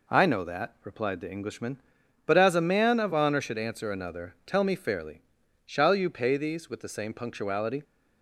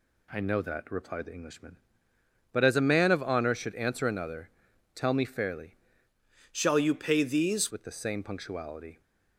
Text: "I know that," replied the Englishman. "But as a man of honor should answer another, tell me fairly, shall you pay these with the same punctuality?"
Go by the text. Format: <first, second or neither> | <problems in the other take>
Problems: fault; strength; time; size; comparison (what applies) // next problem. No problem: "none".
first | changes voice from "shall" to "these"; from 6.5 to 7.6 s; 1.1 s long